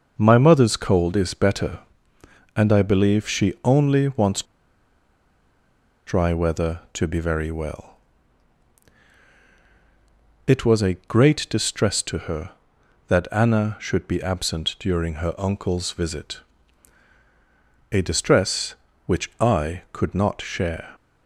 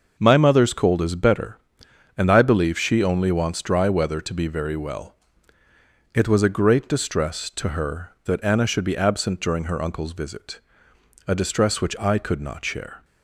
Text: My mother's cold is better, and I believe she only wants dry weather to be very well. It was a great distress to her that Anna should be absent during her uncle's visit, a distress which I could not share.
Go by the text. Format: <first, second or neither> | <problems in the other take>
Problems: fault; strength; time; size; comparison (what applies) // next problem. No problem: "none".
second | pauses between "wants" and "dry"; strong; at 4.4 s; 1.6 s long